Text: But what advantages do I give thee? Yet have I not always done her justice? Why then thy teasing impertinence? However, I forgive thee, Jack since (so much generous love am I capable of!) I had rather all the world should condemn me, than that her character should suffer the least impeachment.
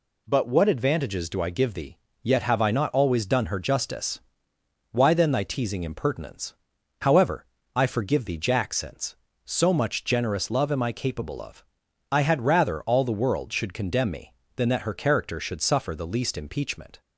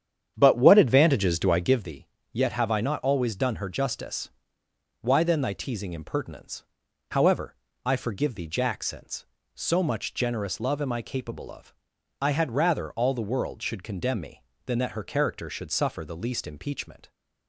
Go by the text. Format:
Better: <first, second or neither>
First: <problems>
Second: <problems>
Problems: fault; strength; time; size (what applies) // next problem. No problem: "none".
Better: first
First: none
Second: starts louder than the rest; strong; until 1.9 s; 9 dB